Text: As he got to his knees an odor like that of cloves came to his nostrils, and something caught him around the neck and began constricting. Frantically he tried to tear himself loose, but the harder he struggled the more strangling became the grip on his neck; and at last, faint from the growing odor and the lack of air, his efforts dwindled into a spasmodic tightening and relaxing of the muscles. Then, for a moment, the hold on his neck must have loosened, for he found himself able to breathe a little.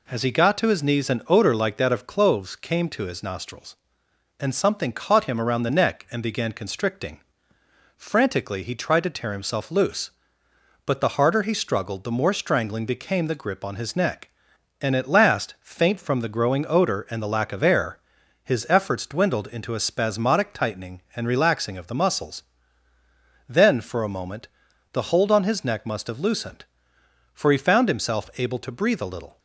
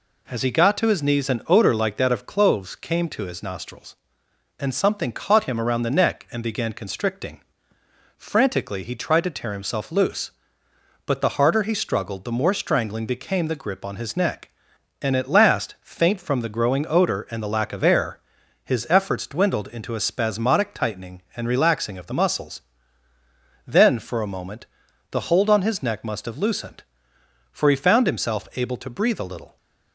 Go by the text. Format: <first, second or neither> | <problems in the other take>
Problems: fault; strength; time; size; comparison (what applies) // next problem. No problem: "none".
neither | none